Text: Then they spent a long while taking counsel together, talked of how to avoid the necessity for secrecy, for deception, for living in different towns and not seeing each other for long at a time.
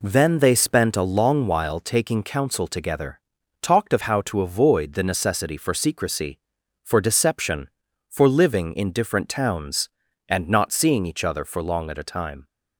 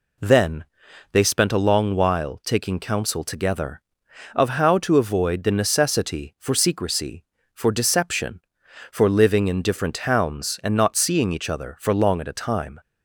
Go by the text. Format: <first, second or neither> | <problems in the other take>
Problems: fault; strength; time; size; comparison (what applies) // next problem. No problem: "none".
first | pauses between "Then" and "they"; noticeable; at 0.6 s; 0.46 s long // skips "talked"; at 4.0 s